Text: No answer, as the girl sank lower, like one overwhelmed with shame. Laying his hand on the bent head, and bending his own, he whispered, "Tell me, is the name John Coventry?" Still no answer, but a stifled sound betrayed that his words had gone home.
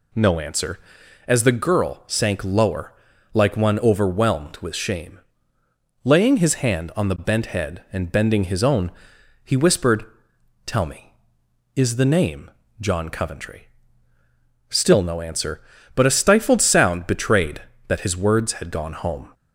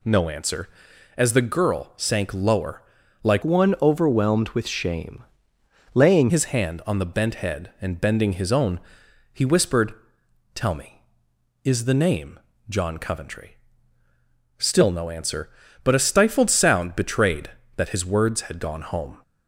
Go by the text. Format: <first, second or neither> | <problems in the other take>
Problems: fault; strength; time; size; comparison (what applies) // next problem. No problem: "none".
first | changes voice from "one" to "Laying"; from 3.4 to 6.3 s; 2.9 s long // pauses between "name" and "John"; slight; at 12.4 s; 0.28 s long; slight in the first